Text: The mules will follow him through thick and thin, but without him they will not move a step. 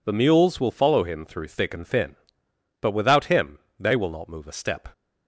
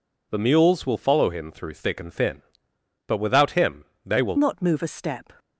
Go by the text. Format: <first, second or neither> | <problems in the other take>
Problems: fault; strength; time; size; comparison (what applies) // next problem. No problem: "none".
first | pauses between "him" and "they"; slight; at 3.8 s; 0.20 s long; slight in the first // changes voice at "not"; from 4.3 s on; 1.0 s long